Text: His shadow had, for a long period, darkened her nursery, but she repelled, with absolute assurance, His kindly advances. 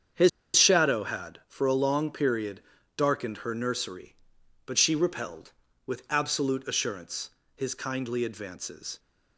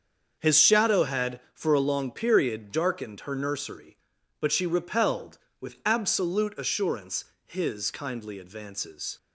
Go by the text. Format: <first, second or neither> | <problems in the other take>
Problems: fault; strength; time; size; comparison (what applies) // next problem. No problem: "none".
second | starts louder than the rest; strong; until 1.5 s; 7.5 dB; also in the second // pauses between "His" and "shadow"; slight; at 0.2 s; 0.26 s long